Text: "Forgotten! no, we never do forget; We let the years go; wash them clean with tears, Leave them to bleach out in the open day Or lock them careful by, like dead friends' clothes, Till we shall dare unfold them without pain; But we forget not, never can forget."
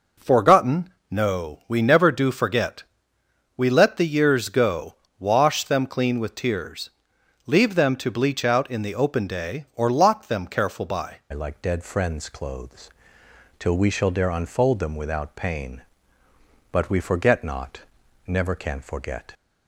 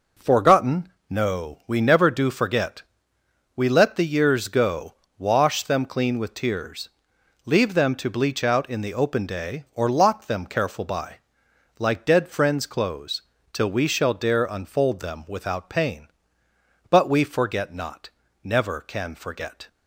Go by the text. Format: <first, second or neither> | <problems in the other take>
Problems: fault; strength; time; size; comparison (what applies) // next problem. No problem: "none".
second | changes voice at "like"; from 11.3 s on; 8.0 s long